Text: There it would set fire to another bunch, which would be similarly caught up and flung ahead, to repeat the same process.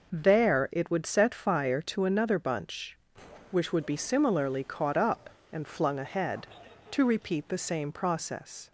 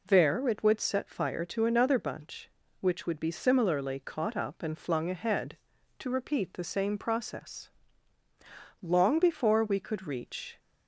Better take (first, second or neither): first